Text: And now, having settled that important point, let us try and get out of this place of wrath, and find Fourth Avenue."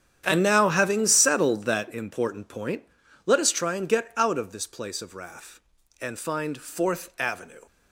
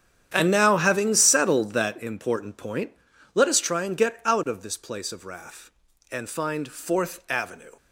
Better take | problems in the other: neither | starts louder than the rest; strong; the same in both

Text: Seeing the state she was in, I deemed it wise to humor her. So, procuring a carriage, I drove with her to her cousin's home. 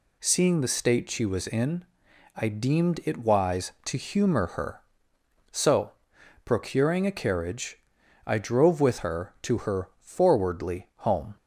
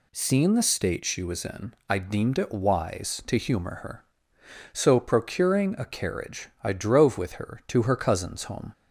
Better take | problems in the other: second | says "forwardly" for "cousin's"; at 9.9 s

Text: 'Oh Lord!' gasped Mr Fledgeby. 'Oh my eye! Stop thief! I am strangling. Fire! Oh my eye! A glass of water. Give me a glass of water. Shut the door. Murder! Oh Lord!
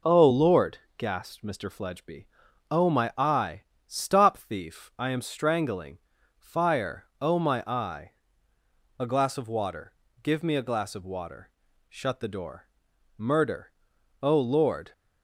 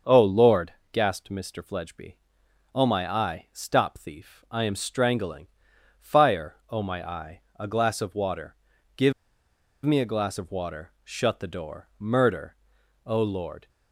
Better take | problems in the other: first | starts louder than the rest; until 1.2 s; 6.5 dB // pauses between "Give" and "me"; noticeable; at 9.1 s; 0.73 s long

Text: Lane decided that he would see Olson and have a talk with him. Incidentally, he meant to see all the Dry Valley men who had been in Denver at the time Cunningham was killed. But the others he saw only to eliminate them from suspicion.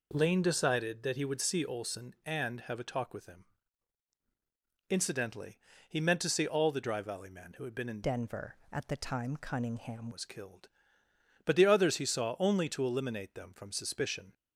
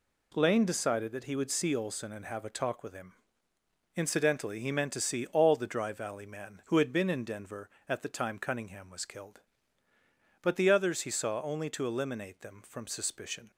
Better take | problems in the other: second | changes voice from "Denver" to "Cunningham"; from 8.0 to 10.1 s; 2.1 s long

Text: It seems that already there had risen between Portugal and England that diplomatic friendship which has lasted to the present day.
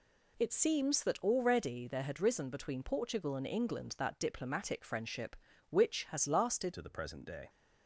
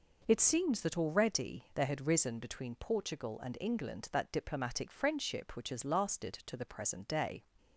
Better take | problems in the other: second | changes voice at "to"; from 6.7 s on; 0.7 s long

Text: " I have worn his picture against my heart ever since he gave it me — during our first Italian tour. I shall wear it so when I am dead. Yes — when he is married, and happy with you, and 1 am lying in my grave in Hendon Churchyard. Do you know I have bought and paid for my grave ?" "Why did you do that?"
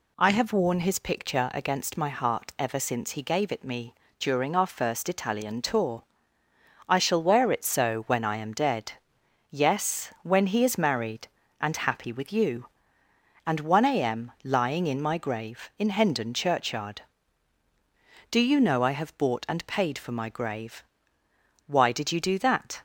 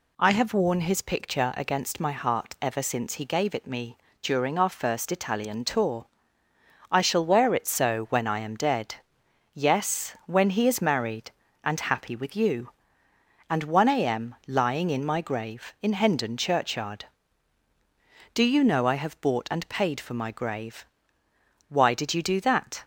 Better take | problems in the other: neither | none

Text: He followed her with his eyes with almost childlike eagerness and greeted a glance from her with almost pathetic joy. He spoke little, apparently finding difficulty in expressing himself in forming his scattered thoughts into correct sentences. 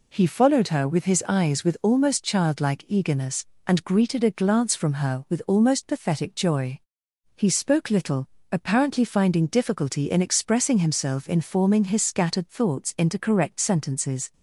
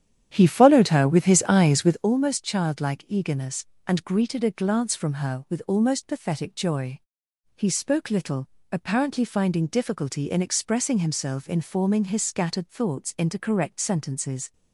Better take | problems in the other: first | starts louder than the rest; strong; until 2.1 s; 10 dB

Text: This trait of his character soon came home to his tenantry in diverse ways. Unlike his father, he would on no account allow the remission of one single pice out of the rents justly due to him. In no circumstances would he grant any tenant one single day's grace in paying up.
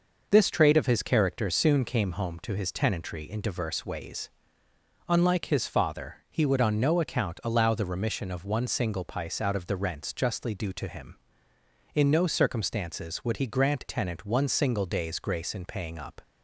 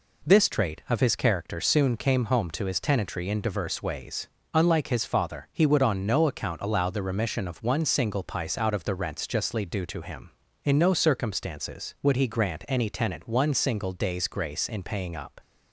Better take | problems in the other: second | skips "any"; at 13.8 s

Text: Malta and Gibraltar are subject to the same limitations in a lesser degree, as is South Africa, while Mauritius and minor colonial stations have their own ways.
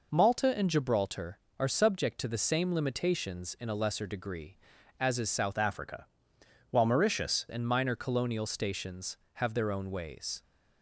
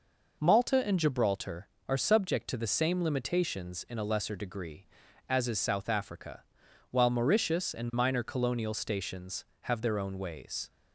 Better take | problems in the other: second | changes voice from "Africa" to "Mauritius"; from 5.5 to 7.4 s; 1.9 s long

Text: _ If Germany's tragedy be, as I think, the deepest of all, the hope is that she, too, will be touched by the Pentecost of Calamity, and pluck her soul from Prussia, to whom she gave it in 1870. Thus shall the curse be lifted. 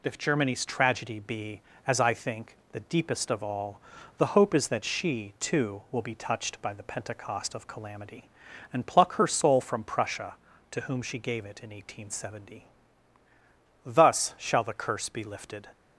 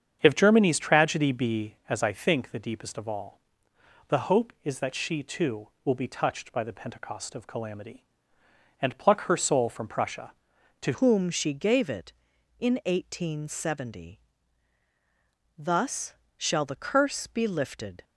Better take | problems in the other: first | starts louder than the rest; strong; until 1.2 s; 7.5 dB // changes voice at "whom"; from 10.9 s on; 7.1 s long // pauses between "Thus" and "shall"; slight; at 16.1 s; 0.24 s long

